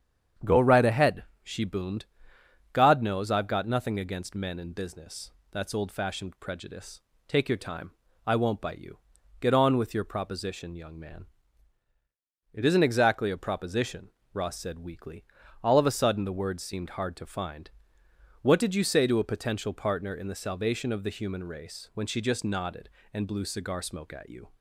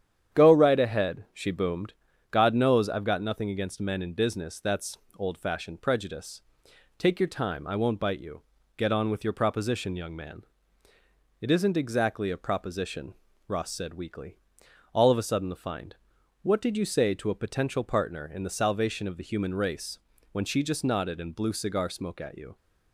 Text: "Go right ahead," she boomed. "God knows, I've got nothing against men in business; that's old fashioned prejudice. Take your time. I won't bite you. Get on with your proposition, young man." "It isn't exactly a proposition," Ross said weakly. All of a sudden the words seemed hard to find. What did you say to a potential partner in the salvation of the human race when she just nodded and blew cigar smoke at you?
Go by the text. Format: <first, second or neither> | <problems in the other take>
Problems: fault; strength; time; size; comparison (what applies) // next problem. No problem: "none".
first | starts louder than the rest; strong; until 1.4 s; 9 dB; strong in the first // pauses between "that's" and "old"; slight; at 4.9 s; 0.22 s long // skips "words seemed hard to"; at 15.5 s // pauses between "race" and "when"; slight; at 19.9 s; 0.34 s long